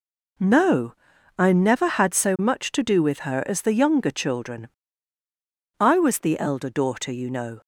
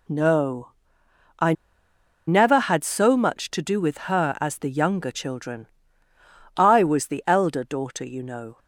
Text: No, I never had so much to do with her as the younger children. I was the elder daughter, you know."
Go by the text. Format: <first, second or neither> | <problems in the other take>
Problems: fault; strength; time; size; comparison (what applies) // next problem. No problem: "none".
first | pauses between "I" and "never"; noticeable; at 1.5 s; 0.75 s long